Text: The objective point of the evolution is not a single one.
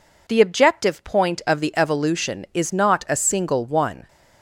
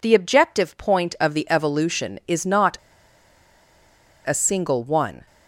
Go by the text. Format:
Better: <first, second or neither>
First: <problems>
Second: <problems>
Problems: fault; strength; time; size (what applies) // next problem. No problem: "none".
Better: first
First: none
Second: pauses between "not" and "a"; strong; at 2.7 s; 1.5 s long